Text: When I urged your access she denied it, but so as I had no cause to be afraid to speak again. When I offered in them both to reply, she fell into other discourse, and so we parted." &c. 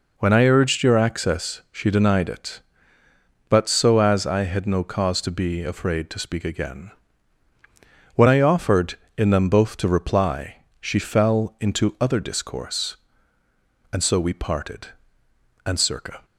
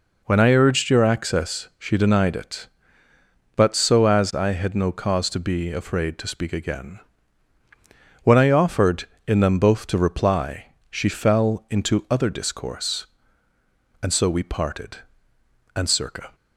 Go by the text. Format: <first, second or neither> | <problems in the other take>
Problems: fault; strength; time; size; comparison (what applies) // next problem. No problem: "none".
neither | none